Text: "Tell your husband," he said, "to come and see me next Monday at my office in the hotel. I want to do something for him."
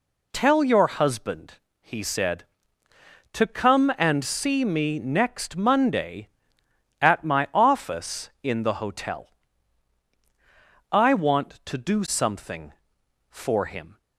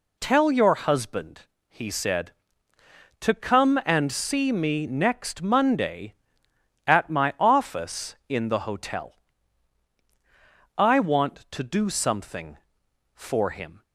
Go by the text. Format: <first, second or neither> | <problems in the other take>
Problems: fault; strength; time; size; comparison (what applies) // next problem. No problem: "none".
neither | none